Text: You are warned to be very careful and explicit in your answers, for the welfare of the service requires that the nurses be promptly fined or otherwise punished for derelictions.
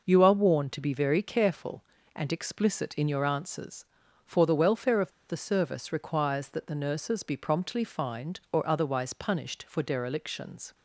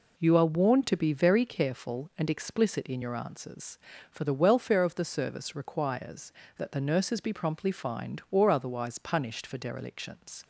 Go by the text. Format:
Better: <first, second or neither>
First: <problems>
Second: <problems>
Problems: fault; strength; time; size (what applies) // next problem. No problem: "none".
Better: second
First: pauses between "of" and "the"; slight; at 5.1 s; 0.17 s long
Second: none